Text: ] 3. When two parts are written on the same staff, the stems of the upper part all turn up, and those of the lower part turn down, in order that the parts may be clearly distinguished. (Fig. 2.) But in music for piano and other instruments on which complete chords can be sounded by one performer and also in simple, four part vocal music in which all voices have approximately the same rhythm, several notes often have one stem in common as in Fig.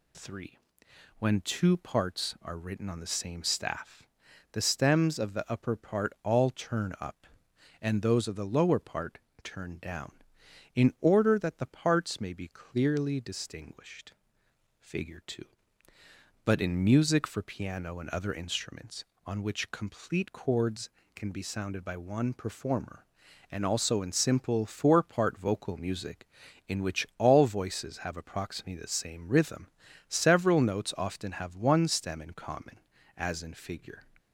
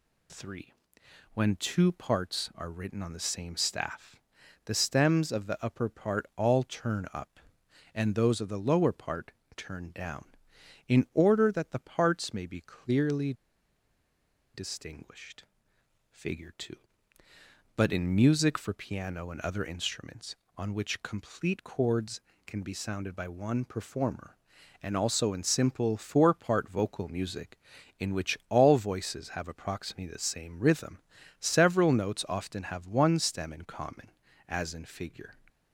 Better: first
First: pauses between "part" and "turn"; slight; at 9.1 s; 0.26 s long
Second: pauses between "part" and "turn"; slight; at 9.3 s; 0.26 s long // pauses between "clearly" and "distinguished"; at 13.3 s; 1.2 s long

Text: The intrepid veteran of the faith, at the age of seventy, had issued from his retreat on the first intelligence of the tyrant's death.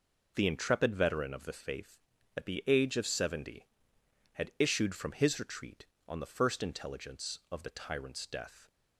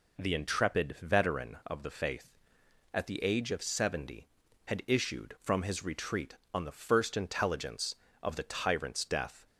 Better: neither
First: none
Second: none

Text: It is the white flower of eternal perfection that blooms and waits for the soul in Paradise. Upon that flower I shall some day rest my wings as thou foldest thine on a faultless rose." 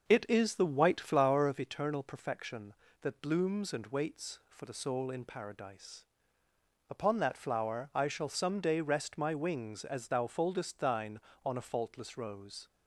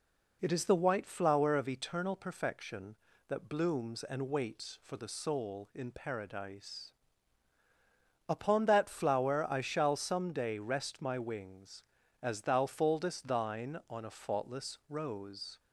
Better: second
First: starts louder than the rest; noticeable; until 1.7 s; 6 dB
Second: none

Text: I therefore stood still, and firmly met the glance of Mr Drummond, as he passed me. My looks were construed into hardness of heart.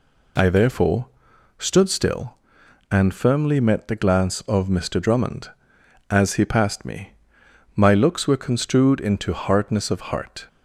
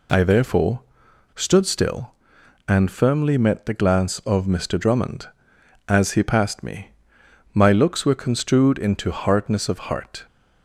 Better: neither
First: pauses between "therefore" and "stood"; noticeable; at 1.0 s; 0.50 s long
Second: pauses between "therefore" and "stood"; noticeable; at 0.8 s; 0.52 s long

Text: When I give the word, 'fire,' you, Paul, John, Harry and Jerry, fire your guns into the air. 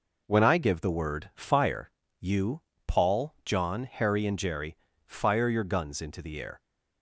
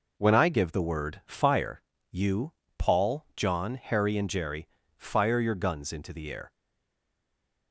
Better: first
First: none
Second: stays silent after the last word; noticeable; from 6.5 s on; 1.2 s long

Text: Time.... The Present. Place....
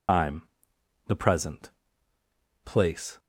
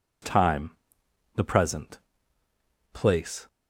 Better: second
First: loses the start of "Time"; at 0.0 s; 150 ms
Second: none

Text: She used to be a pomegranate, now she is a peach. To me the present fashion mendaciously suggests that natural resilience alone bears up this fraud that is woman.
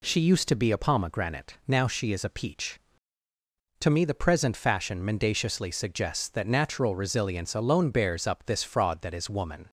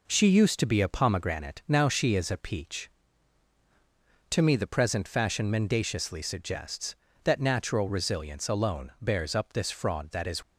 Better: first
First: none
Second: stops before "woman"; at 10.4 s

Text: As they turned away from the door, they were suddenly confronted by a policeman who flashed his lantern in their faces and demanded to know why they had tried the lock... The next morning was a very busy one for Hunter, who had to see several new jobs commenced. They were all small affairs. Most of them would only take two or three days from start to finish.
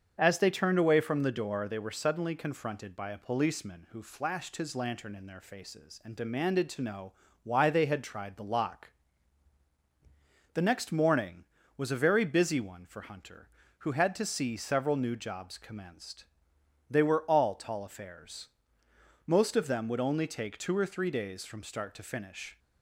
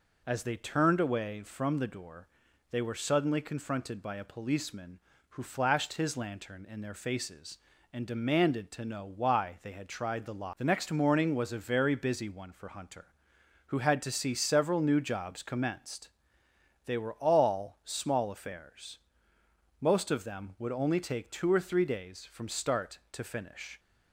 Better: second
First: starts louder than the rest; until 1.1 s; 7 dB // pauses between "know" and "why"; slight; at 7.1 s; 0.32 s long // says "tall" for "small"; at 17.5 s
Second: none

